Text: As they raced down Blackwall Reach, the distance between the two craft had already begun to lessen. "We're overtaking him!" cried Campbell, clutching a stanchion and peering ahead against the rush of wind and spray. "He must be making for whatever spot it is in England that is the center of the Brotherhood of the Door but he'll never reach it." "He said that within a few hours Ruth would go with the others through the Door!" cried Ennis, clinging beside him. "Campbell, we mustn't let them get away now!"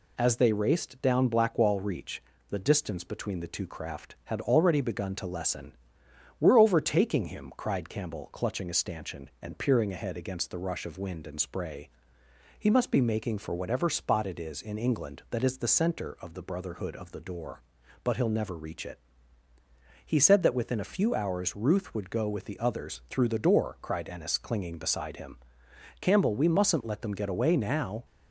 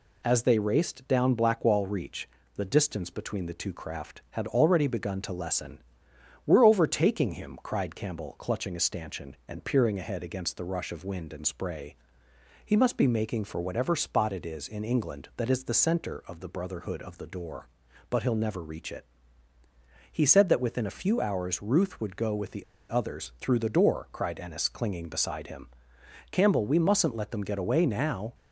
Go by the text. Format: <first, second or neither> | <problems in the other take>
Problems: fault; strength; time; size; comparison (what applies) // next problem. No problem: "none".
first | pauses between "the" and "others"; slight; at 22.6 s; 0.25 s long